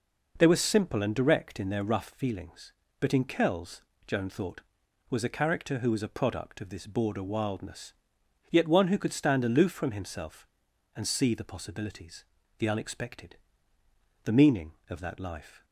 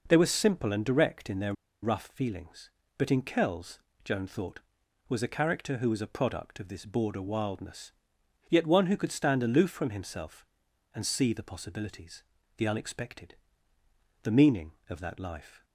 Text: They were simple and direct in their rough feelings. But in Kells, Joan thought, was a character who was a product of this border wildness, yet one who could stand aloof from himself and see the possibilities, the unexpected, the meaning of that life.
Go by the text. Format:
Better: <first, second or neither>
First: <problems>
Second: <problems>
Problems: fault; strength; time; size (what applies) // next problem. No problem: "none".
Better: first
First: none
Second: pauses between "their" and "rough"; slight; at 1.5 s; 0.30 s long